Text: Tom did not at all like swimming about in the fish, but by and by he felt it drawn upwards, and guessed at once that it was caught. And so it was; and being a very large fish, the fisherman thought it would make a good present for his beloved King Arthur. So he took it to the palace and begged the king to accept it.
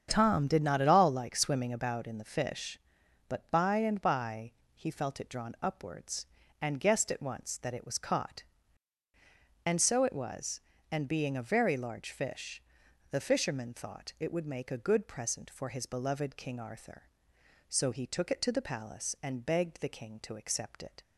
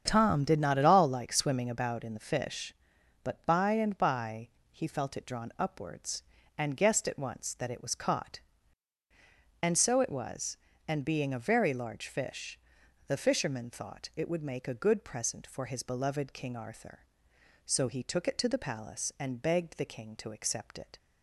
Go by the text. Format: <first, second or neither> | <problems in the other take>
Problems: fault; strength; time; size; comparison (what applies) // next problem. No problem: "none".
neither | starts louder than the rest; strong; the same in both // pauses between "by" and "he"; slight; the same in both